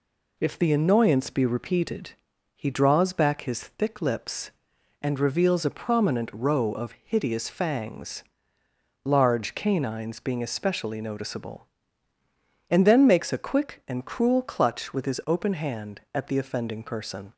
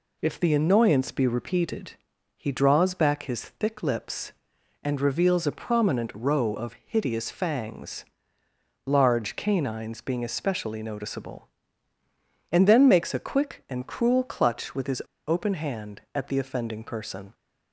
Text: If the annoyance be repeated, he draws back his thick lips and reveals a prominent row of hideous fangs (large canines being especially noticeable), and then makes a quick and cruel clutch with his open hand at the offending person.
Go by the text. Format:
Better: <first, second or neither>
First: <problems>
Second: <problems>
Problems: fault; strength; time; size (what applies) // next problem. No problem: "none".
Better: first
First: none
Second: pauses between "his" and "open"; slight; at 15.0 s; 0.26 s long